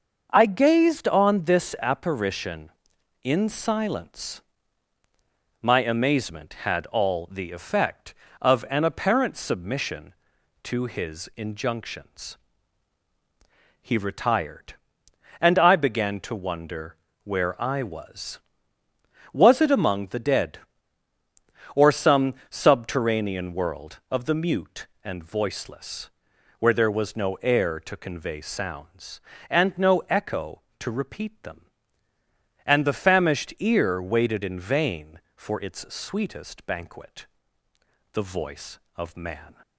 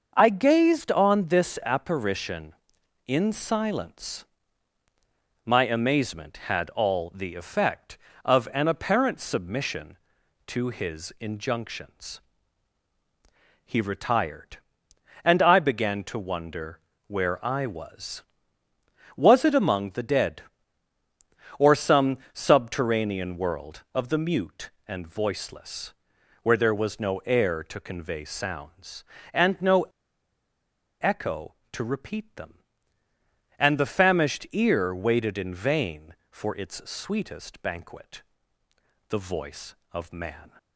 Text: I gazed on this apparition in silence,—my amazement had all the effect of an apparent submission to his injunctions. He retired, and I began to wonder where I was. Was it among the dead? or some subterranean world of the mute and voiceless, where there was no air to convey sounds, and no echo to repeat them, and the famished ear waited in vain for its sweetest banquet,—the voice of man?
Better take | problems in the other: first | starts louder than the rest; until 1.1 s; 6.5 dB; also in the first // pauses between "wonder" and "where"; slight; at 16.7 s; 0.28 s long; slight in the first // pauses between "some" and "subterranean"; slight; at 22.1 s; 0.16 s long; slight in the first // pauses between "no" and "echo"; at 29.8 s; 1.1 s long

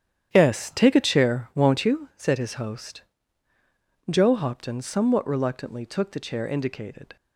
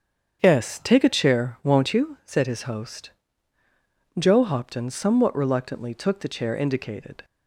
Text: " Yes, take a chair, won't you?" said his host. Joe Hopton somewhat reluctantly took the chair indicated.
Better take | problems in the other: second | gets quieter; strong; throughout; 11.5 dB // starts louder than the rest; strong; until 1.3 s; 10 dB; strong in the second

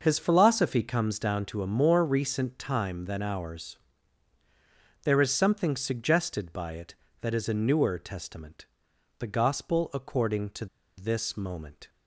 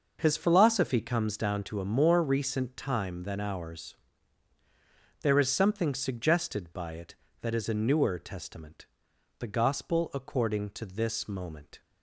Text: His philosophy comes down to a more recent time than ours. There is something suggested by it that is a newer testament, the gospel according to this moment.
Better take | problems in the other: second | starts louder than the rest; noticeable; until 1.0 s; 6 dB; noticeable in the second // pauses between "to" and "this"; slight; at 10.6 s; 0.31 s long

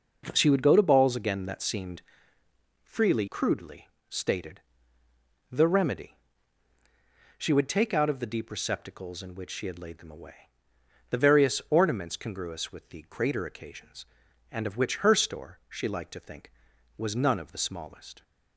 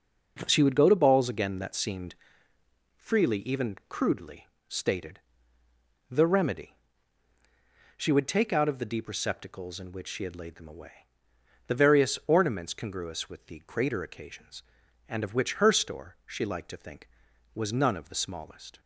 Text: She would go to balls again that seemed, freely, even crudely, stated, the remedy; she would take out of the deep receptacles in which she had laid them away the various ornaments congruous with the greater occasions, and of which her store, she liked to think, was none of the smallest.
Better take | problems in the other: second | skips "even"; at 3.2 s // pauses between "away" and "the"; noticeable; at 10.5 s; 0.60 s long; noticeable in the second

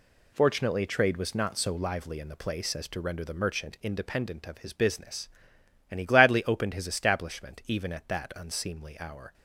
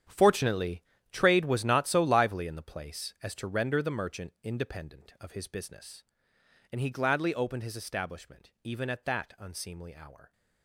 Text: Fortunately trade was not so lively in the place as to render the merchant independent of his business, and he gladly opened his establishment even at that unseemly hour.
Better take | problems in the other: first | gets quieter; strong; throughout; 14 dB // pauses between "Fortunately" and "trade"; slight; at 0.8 s; 0.30 s long

